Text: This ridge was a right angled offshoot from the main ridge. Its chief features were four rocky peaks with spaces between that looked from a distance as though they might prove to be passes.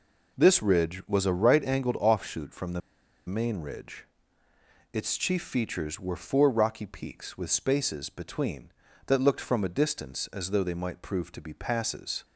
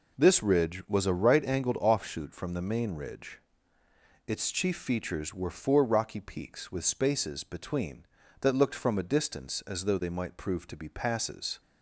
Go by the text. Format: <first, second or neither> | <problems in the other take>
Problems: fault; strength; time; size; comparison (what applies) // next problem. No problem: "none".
second | pauses between "the" and "main"; noticeable; at 2.8 s; 0.46 s long